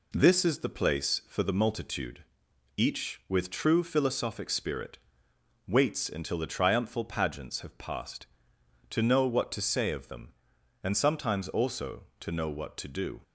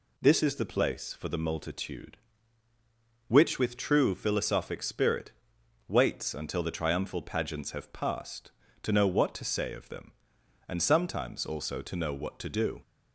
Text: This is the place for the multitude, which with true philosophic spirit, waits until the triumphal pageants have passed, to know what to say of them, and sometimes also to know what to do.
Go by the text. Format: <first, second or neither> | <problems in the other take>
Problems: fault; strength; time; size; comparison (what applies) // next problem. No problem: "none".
second | says "each" for "which"; at 2.7 s